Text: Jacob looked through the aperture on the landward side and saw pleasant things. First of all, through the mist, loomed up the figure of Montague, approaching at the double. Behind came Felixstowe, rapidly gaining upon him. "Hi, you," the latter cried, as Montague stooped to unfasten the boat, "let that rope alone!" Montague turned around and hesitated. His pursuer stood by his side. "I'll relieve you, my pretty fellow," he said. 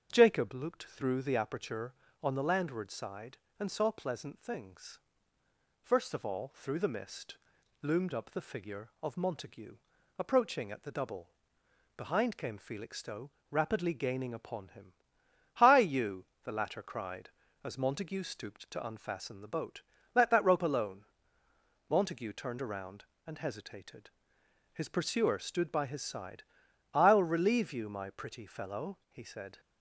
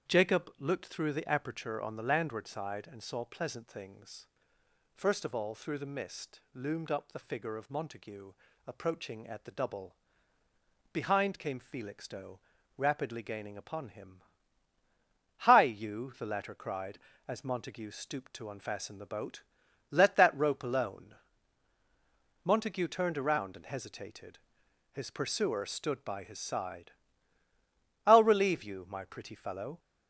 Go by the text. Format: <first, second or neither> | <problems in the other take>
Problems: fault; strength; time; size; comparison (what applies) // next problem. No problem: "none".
first | starts louder than the rest; strong; until 1.1 s; 8 dB; also in the first // stops before "he said"; at 29.7 s